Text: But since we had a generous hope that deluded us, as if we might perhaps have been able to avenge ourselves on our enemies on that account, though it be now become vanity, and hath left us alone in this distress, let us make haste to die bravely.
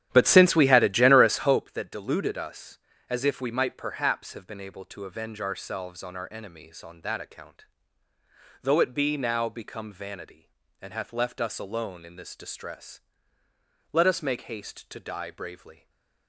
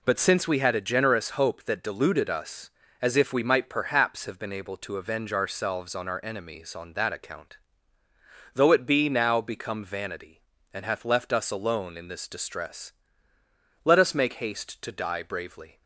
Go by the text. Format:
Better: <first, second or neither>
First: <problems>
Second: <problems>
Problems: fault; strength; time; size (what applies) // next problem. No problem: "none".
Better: second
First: starts louder than the rest; strong; until 1.7 s; 11 dB // stays silent after the last word; slight; from 15.7 s on; 0.5 s long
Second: none